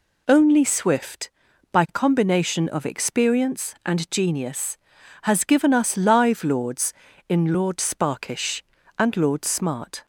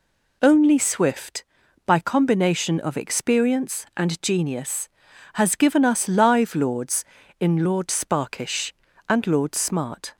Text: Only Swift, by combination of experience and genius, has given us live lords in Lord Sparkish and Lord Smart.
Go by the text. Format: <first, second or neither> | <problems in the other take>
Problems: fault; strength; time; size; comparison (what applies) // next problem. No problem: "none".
neither | none